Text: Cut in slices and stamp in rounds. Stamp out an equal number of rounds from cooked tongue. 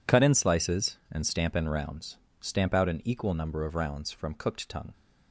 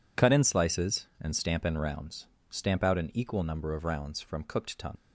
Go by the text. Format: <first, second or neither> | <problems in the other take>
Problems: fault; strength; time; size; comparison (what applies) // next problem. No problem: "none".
first | leaves "tongue" unfinished; at 4.9 s; 60 ms